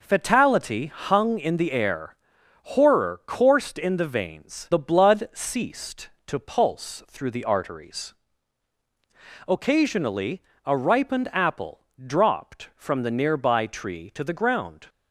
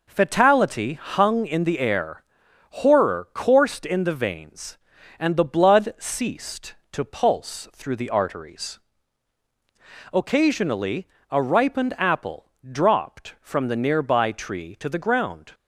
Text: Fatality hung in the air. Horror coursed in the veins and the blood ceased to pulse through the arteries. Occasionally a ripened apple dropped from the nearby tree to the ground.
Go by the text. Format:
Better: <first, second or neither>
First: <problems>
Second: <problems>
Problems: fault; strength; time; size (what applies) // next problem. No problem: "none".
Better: second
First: skips "and"; at 4.7 s // pauses between "Occasionally" and "a"; slight; at 10.4 s; 0.24 s long // pauses between "apple" and "dropped"; slight; at 11.8 s; 0.22 s long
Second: pauses between "Occasionally" and "a"; slight; at 11.0 s; 0.24 s long // pauses between "apple" and "dropped"; slight; at 12.4 s; 0.22 s long